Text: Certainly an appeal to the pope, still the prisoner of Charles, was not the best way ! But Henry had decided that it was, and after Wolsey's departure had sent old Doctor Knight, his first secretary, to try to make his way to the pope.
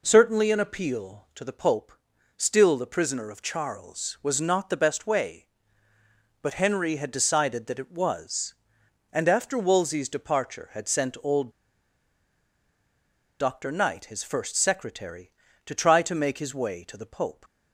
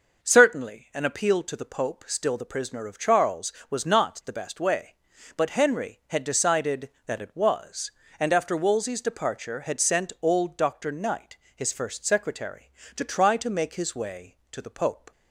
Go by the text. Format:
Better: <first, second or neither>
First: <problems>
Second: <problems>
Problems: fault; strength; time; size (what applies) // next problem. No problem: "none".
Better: second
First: pauses between "old" and "Doctor"; strong; at 11.5 s; 1.8 s long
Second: none